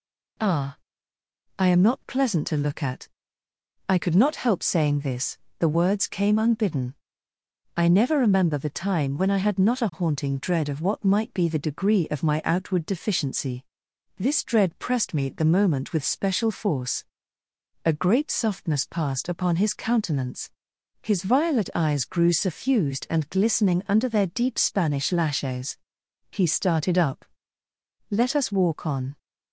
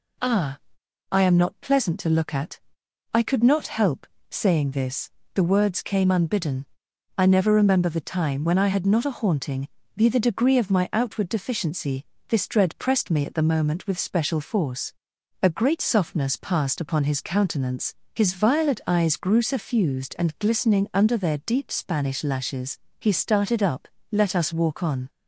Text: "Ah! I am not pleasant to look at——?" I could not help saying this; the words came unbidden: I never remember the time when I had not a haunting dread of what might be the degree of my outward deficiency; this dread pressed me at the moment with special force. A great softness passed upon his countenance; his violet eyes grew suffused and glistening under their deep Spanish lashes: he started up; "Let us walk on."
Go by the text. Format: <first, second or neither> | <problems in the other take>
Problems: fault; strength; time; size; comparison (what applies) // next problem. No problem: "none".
first | pauses between "help" and "saying"; slight; at 4.0 s; 0.24 s long // skips "dread of what might"; at 9.8 s